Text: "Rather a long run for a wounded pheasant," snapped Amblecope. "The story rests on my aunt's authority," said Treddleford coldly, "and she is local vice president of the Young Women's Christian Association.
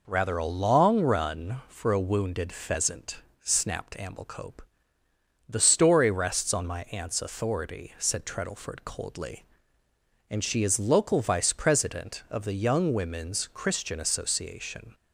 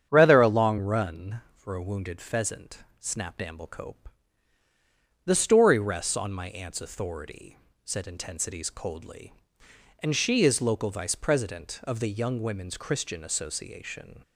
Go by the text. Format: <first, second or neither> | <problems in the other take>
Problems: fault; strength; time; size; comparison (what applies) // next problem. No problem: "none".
first | starts louder than the rest; strong; until 1.1 s; 8.5 dB // says "Intensities" for "Treddleford"; at 8.0 s